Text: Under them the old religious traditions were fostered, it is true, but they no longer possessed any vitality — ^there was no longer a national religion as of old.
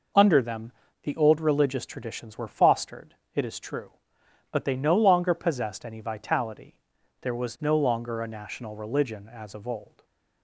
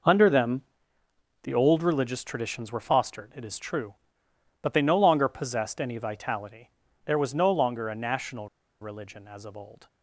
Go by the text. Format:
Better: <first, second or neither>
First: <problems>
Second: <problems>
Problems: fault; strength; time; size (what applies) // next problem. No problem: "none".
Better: first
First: pauses between "them" and "the"; slight; at 0.7 s; 0.30 s long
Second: pauses between "them" and "the"; noticeable; at 0.6 s; 0.82 s long // pauses between "national" and "religion"; slight; at 8.4 s; 0.32 s long